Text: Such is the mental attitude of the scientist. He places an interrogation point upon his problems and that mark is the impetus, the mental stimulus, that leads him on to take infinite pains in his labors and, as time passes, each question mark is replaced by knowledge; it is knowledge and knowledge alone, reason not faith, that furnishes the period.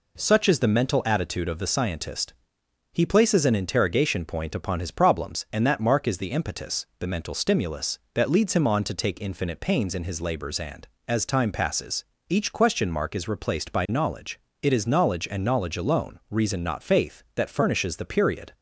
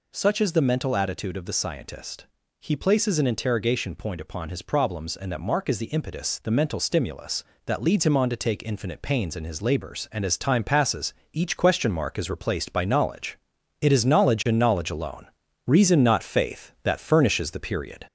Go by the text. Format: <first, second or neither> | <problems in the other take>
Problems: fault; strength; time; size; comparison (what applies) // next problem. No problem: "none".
first | gets louder; slight; throughout; 2.5 dB